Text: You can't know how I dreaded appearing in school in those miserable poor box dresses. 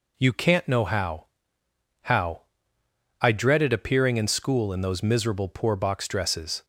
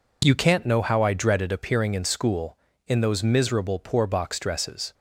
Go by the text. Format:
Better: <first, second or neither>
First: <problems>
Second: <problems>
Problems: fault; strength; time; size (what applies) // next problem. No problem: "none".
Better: second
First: says "how" twice; at 2.0 s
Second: none